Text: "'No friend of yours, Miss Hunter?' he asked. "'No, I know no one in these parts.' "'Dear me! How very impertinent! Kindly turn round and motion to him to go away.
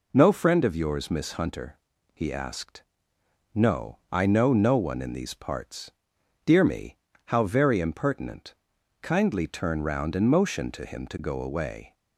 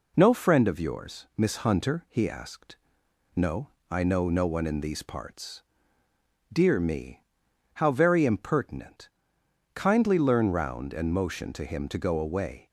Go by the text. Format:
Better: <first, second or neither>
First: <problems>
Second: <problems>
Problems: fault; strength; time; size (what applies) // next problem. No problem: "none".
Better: first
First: none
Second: says "learn" for "turn"; at 10.1 s